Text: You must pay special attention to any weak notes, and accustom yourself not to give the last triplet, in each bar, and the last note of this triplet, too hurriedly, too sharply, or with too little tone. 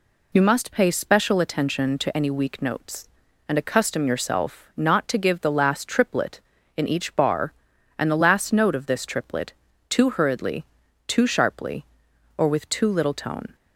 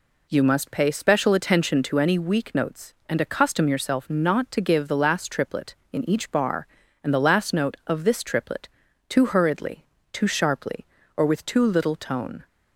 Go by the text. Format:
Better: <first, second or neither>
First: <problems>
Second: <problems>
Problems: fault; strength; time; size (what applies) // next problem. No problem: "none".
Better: neither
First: none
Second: none